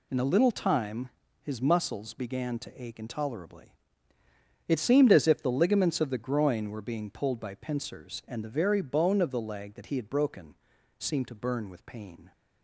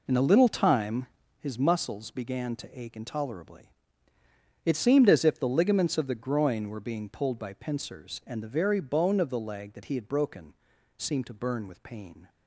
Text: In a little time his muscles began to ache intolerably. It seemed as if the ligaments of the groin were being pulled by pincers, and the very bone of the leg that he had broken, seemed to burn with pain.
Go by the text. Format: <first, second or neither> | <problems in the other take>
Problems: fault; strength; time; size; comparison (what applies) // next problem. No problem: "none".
first | starts louder than the rest; until 1.4 s; 4 dB // pauses between "time" and "his"; slight; at 1.0 s; 0.32 s long; slight in the first